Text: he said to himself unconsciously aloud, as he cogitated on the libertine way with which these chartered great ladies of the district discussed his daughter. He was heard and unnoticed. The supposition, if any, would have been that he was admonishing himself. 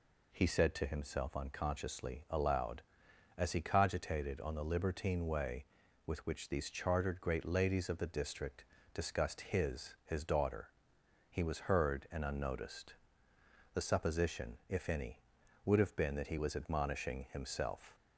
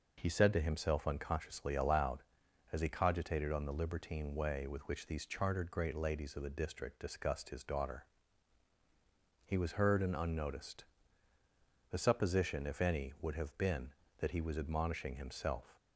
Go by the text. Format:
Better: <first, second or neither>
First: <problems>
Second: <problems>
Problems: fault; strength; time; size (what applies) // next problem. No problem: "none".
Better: second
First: pauses between "district" and "discussed"; slight; at 8.6 s; 0.30 s long // says "his" twice; at 10.0 s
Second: none